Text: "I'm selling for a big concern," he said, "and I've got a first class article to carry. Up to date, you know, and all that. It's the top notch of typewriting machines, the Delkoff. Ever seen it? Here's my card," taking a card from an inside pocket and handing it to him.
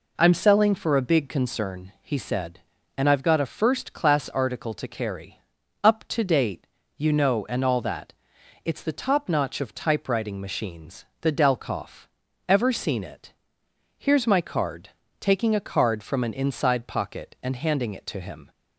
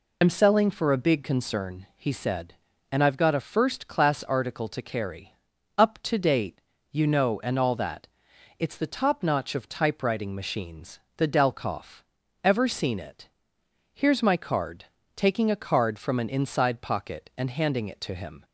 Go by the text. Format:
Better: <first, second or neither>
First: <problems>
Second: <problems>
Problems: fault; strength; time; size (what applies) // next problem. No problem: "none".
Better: first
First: none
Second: loses the start of "I'm"; at 0.2 s; 80 ms